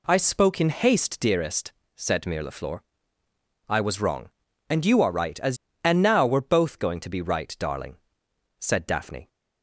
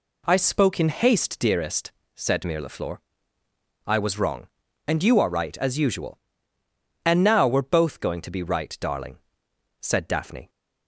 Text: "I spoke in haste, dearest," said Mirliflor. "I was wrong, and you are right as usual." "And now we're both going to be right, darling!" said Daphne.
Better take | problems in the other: second | skips "usual"; at 5.7 s

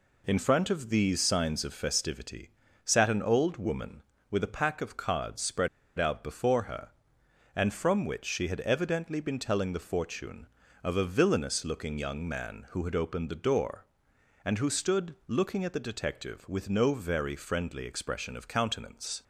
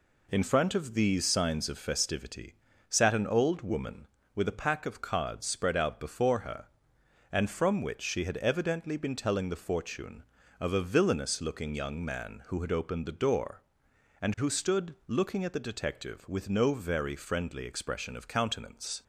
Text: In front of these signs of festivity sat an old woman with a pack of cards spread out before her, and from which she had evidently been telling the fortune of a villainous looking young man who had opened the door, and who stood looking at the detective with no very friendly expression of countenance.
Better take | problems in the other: second | pauses between "festivity" and "sat"; slight; at 2.4 s; 0.34 s long; slight in the second // pauses between "spread" and "out"; slight; at 5.6 s; 0.30 s long

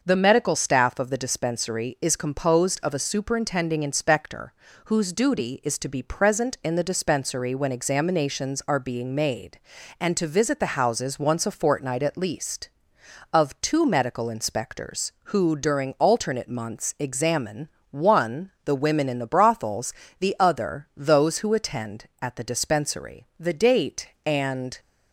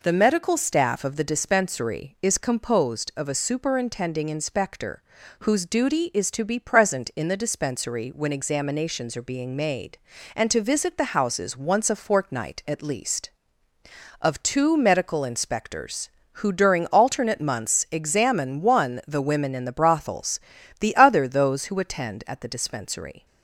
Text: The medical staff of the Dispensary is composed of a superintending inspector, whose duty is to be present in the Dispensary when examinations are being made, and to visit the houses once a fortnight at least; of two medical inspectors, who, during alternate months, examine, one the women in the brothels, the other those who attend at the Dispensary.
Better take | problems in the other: second | starts louder than the rest; until 1.0 s; 6 dB // pauses between "one" and "the"; slight; at 18.4 s; 0.16 s long // goes on to say "The date and"; from 23.3 s on; 1.4 s long

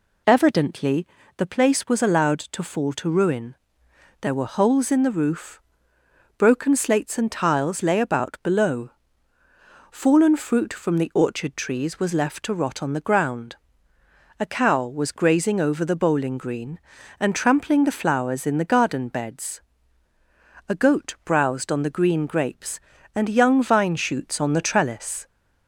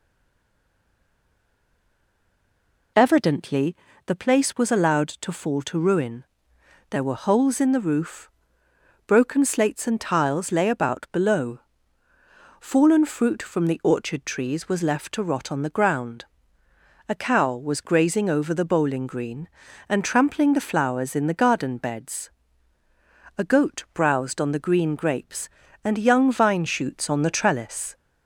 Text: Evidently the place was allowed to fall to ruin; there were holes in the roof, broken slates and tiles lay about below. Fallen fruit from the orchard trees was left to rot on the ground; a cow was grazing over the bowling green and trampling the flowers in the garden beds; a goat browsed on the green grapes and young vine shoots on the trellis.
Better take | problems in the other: first | stays silent before the first word; strong; until 2.9 s; 2.9 s long // pauses between "Evidently" and "the"; slight; at 3.7 s; 0.32 s long; slight in the first

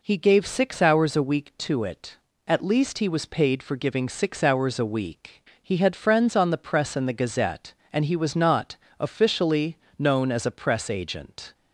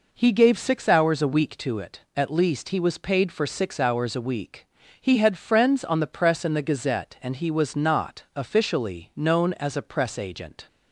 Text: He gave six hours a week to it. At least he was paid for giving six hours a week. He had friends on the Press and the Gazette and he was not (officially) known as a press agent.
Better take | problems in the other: first | skips "giving"; at 3.4 s

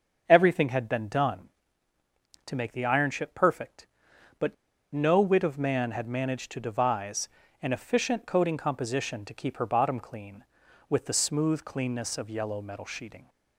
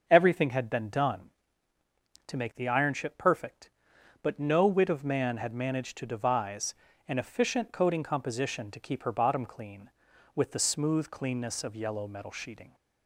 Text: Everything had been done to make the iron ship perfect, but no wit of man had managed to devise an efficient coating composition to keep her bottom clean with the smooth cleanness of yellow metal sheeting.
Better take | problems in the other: second | starts louder than the rest; until 1.2 s; 6.5 dB; also in the second // pauses between "but" and "no"; at 4.5 s; 0.37 s long // pauses between "devise" and "an"; slight; at 7.2 s; 0.34 s long; slight in the second

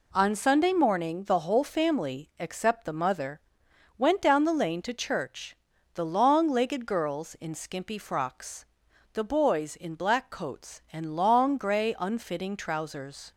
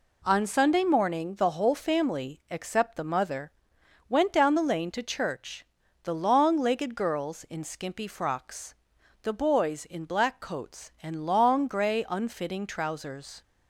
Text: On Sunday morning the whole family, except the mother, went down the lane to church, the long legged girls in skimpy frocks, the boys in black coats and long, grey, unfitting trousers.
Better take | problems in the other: neither | none

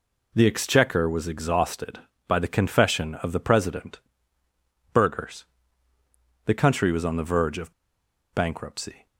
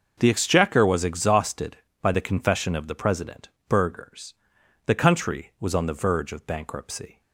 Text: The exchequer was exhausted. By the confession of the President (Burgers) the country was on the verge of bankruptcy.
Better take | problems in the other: second | pauses between "of" and "bankruptcy"; noticeable; at 7.7 s; 0.60 s long

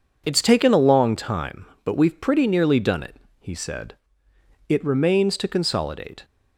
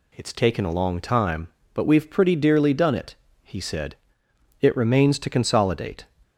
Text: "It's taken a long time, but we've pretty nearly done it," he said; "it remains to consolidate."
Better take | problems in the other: first | says "dearly" for "nearly"; at 2.3 s

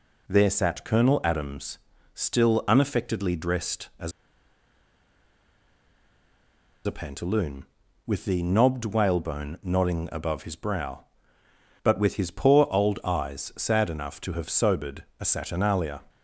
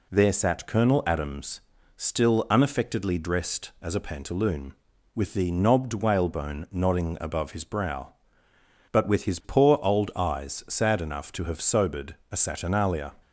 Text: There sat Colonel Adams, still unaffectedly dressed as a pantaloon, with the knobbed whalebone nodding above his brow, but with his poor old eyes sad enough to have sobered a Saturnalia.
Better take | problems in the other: second | pauses between "as" and "a"; strong; at 4.1 s; 2.7 s long // pauses between "sobered" and "a"; slight; at 15.0 s; 0.16 s long; slight in the second

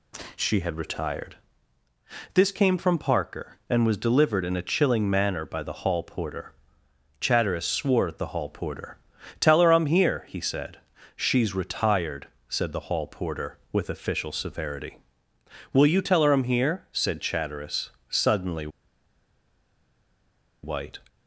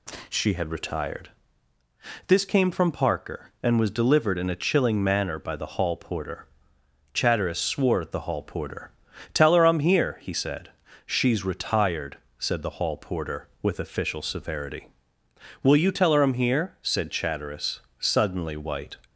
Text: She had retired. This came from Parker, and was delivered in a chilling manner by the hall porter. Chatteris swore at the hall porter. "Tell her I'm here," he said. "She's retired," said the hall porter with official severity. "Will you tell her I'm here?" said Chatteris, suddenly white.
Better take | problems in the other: second | pauses between "suddenly" and "white"; strong; at 18.6 s; 1.9 s long

